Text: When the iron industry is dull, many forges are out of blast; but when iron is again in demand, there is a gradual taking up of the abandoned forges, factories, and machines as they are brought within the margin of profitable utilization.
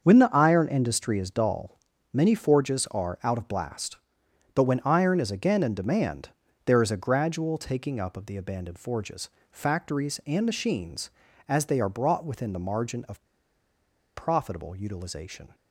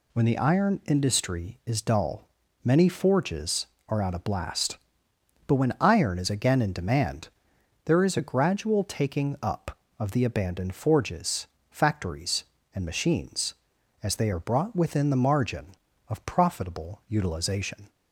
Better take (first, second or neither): second